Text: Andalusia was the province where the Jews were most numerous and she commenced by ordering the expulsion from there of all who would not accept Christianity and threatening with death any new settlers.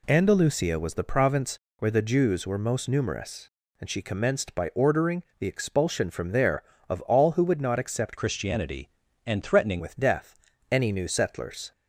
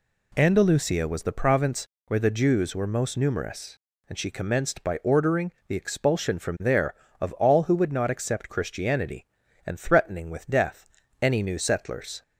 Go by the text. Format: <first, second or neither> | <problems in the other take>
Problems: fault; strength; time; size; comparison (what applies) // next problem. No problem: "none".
second | pauses between "province" and "where"; slight; at 1.5 s; 0.22 s long; slight in the second // pauses between "ordering" and "the"; slight; at 5.2 s; 0.16 s long; slight in the second // changes voice from "Christianity" to "threatening"; from 8.1 to 9.8 s; 1.7 s long // pauses between "death" and "any"; slight; at 10.3 s; 0.36 s long; slight in the second